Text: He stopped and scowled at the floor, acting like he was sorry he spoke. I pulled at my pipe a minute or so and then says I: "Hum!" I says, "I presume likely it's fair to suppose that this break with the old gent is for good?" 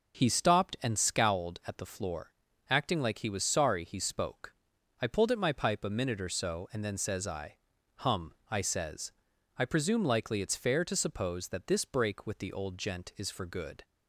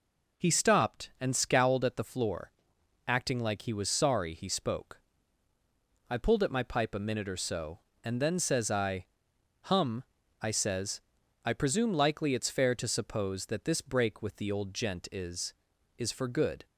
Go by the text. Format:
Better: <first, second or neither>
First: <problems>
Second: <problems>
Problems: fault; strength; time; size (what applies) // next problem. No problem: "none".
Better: first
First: none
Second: says "is" twice; at 15.9 s